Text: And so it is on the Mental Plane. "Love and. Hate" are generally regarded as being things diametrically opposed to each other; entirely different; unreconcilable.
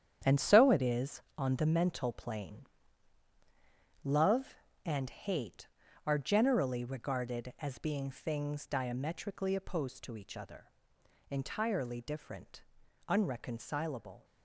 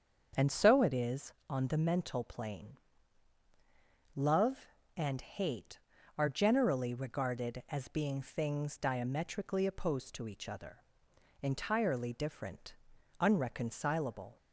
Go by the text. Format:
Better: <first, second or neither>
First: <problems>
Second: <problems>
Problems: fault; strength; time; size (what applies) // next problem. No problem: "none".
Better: second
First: gets quieter; strong; throughout; 10 dB // starts louder than the rest; strong; until 1.4 s; 9 dB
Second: starts louder than the rest; until 1.5 s; 7 dB